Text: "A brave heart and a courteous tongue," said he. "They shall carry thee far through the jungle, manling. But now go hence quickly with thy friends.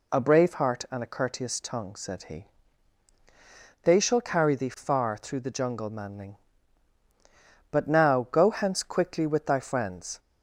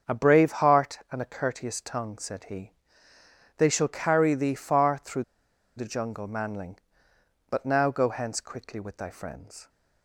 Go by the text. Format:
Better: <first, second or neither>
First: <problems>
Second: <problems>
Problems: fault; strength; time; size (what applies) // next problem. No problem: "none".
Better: first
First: none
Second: starts louder than the rest; until 1.1 s; 6.5 dB // pauses between "through" and "the"; noticeable; at 5.2 s; 0.52 s long